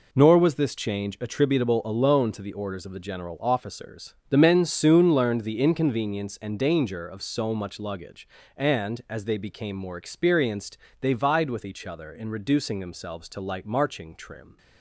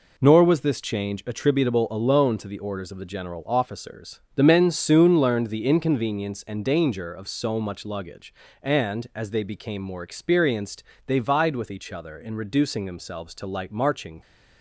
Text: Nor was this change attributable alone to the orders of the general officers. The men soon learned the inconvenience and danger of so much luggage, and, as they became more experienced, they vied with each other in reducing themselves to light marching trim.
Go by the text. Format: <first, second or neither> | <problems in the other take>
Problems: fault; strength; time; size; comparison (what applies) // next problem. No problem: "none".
first | stops before "trim"; at 14.2 s